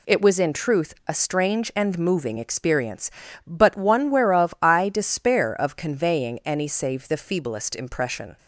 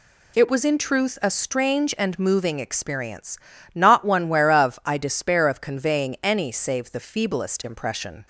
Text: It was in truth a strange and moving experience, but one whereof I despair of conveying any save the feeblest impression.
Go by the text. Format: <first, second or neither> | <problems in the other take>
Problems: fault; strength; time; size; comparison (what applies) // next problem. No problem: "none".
first | says "not" for "but"; at 3.7 s